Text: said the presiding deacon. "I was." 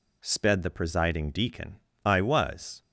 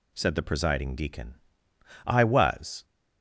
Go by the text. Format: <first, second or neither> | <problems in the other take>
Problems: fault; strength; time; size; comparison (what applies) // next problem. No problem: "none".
second | says "sped" for "said"; at 0.2 s